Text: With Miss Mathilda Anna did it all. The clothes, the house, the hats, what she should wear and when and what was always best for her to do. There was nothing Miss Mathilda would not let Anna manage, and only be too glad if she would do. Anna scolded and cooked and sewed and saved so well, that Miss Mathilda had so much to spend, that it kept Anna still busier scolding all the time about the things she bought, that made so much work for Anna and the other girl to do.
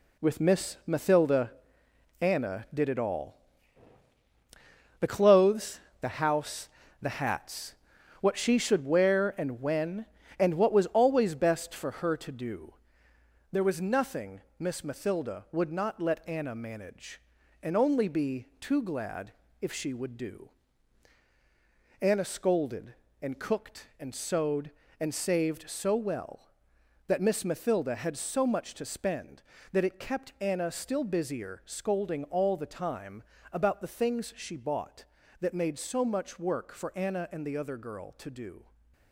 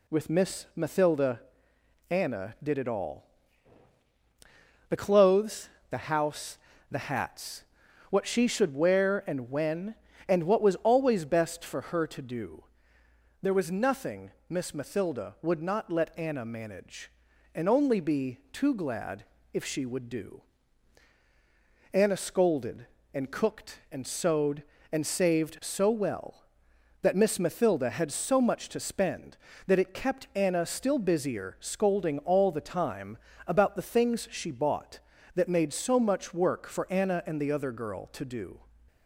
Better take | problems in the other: second | gets quieter; throughout; 7 dB // pauses between "Mathilda" and "Anna"; noticeable; at 1.5 s; 0.68 s long; noticeable in the second // pauses between "nothing" and "Miss"; slight; at 14.4 s; 0.18 s long; slight in the second // pauses between "glad" and "if"; slight; at 19.3 s; 0.28 s long; slight in the second // pauses between "time" and "about"; slight; at 33.2 s; 0.32 s long; slight in the second

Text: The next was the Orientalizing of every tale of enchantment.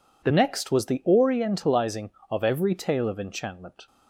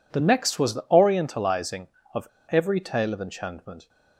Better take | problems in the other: first | pauses between "of" and "every"; slight; at 2.2 s; 0.23 s long

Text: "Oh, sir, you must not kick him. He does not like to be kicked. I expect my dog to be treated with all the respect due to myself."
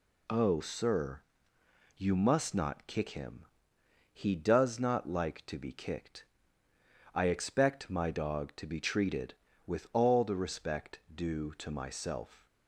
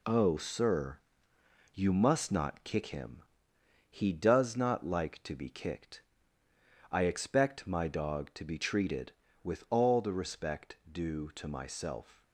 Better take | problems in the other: first | gets quieter; noticeable; throughout; 6 dB

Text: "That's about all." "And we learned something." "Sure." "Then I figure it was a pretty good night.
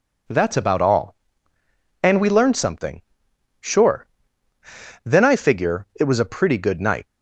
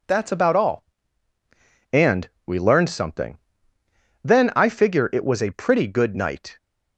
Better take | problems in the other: first | pauses between "And" and "we"; slight; at 2.2 s; 0.18 s long // skips "Sure"; at 3.7 s

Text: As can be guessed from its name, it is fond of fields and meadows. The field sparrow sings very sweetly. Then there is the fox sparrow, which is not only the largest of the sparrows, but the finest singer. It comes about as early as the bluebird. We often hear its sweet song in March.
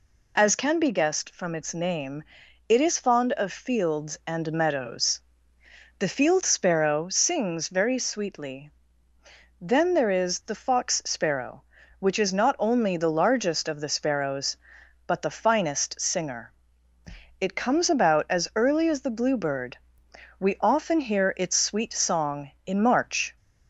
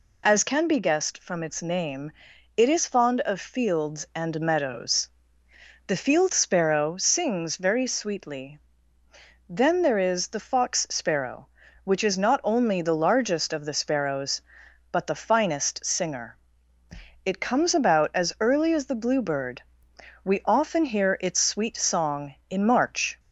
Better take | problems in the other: neither | none

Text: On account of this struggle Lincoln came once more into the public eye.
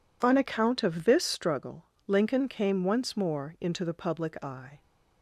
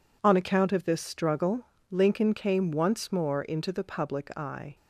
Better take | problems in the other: neither | pauses between "struggle" and "Lincoln"; slight; the same in both

